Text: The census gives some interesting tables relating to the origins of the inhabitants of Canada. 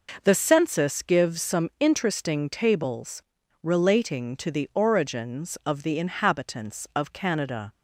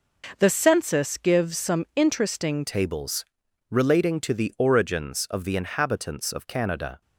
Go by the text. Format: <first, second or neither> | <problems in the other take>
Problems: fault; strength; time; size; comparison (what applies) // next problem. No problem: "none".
first | changes voice at "tables"; from 2.6 s on; 4.4 s long // pauses between "tables" and "relating"; at 3.2 s; 0.44 s long; also in the first